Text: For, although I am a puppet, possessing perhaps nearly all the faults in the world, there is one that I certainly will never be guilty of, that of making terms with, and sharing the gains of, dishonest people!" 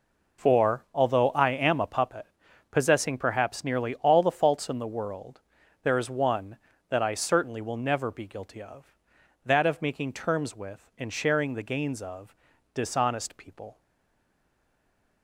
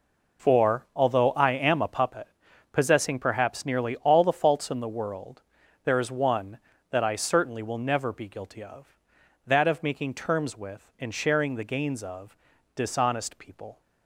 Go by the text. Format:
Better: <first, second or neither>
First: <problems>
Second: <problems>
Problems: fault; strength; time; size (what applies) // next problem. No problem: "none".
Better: second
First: stays silent after the last word; noticeable; from 13.7 s on; 1.5 s long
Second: none